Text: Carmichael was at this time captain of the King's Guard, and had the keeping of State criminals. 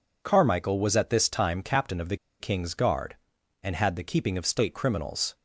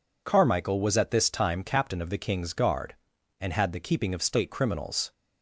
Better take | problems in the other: second | pauses between "the" and "King's"; slight; at 2.1 s; 0.24 s long

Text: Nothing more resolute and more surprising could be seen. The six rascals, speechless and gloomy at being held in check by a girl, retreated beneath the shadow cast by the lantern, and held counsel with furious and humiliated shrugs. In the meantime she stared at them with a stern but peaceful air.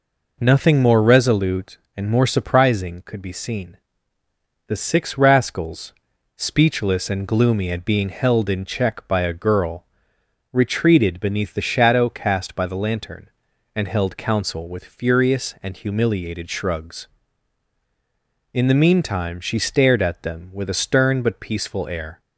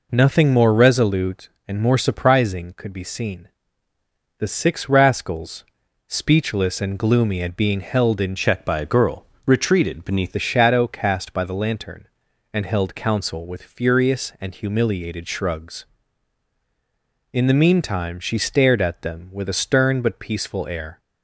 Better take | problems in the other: first | changes voice from "check" to "beneath"; from 8.3 to 10.3 s; 2.0 s long

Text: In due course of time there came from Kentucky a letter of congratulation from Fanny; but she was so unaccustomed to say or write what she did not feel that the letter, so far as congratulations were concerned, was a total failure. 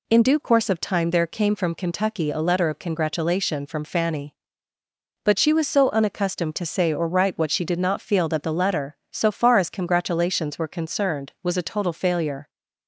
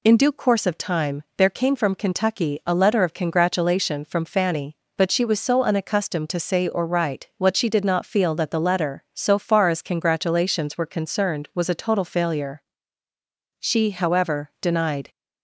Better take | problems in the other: first | pauses between "time" and "there"; slight; at 1.2 s; 0.16 s long // goes on to say "She however denied"; from 13.5 s on; 1.5 s long

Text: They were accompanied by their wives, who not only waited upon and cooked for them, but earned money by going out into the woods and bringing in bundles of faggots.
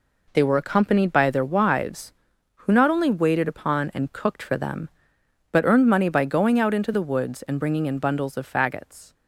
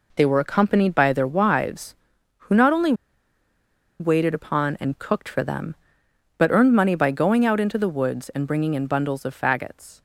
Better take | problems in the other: first | pauses between "only" and "waited"; at 2.9 s; 1.0 s long

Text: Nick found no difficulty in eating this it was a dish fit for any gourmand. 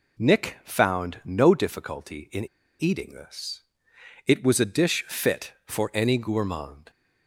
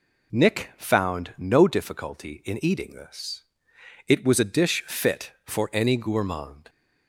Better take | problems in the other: second | pauses between "in" and "eating"; slight; at 2.4 s; 0.34 s long // pauses between "this" and "it"; noticeable; at 3.5 s; 0.66 s long; noticeable in the second

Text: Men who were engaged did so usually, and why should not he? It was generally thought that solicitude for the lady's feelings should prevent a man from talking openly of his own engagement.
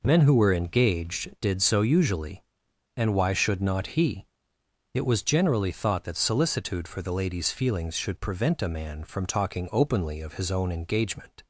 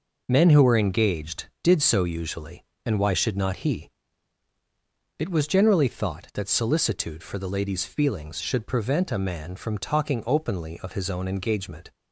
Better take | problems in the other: neither | none

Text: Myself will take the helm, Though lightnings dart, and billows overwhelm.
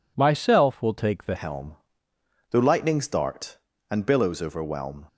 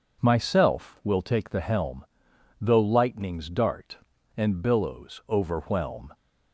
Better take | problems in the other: second | changes voice at "helm"; from 1.3 s on; 3.7 s long

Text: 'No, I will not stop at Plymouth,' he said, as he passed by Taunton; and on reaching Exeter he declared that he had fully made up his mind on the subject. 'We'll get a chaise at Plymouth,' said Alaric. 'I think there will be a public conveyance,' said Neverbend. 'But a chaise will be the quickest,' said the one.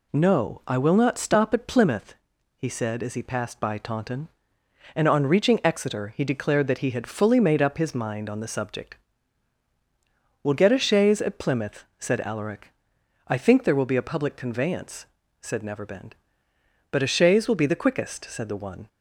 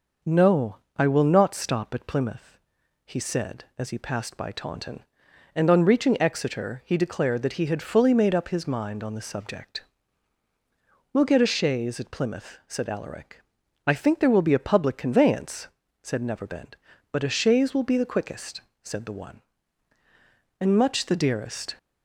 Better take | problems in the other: first | goes on to say "And much the dearest"; noticeable; from 20.5 s on; 1.1 s long

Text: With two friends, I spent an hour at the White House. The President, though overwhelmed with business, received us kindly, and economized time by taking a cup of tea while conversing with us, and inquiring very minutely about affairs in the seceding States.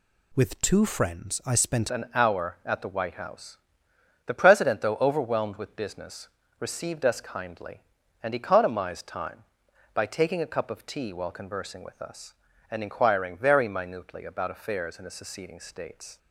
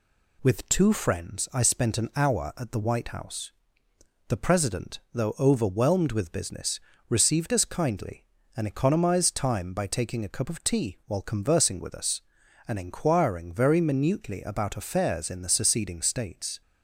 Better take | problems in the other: second | changes voice at "an"; from 1.8 s on; 14.3 s long

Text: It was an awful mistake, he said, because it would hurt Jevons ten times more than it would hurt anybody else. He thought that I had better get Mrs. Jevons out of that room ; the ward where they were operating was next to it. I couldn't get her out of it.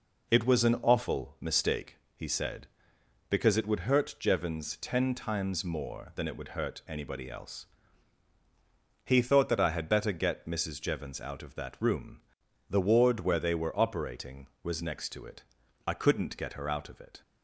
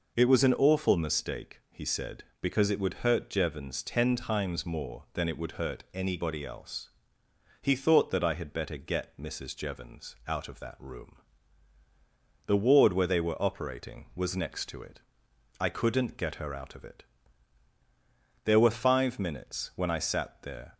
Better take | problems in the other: first | goes on to say "There were five minutes when I sat there"; strong; from 18.4 s on; 2.3 s long

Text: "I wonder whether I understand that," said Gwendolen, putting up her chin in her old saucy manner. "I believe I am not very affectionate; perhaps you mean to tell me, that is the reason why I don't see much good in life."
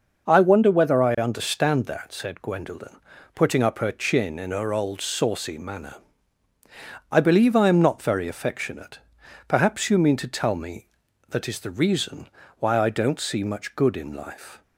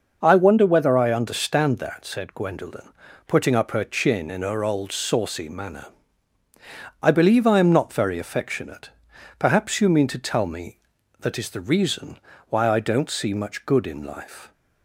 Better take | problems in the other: neither | pauses between "reason" and "why"; slight; the same in both

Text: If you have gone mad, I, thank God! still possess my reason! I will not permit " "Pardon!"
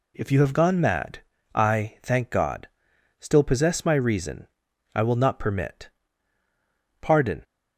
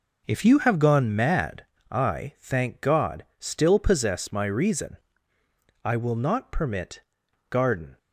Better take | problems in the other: first | says "Garden" for "Pardon"; at 7.4 s

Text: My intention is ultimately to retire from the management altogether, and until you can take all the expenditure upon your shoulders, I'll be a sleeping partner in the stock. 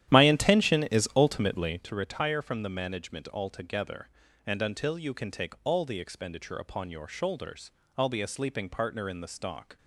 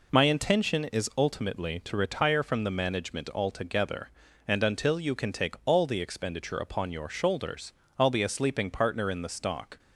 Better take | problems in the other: second | starts louder than the rest; strong; until 1.9 s; 11.5 dB

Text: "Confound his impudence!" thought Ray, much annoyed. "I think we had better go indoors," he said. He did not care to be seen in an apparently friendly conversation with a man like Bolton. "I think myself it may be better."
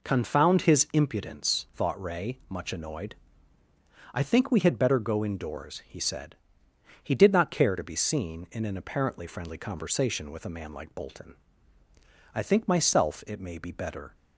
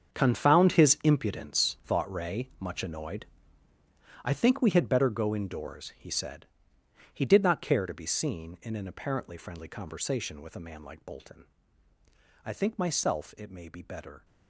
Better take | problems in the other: first | gets quieter; strong; throughout; 13.5 dB

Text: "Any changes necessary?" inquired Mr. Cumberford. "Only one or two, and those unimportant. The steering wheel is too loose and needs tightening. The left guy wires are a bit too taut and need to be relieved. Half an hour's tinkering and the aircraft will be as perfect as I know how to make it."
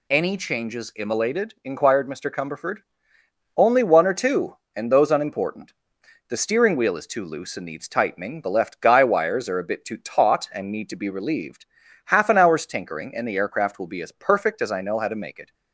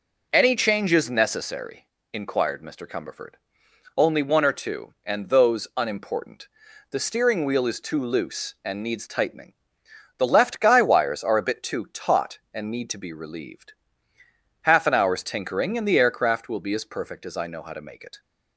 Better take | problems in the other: second | says "immolated" for "necessary"; at 0.9 s

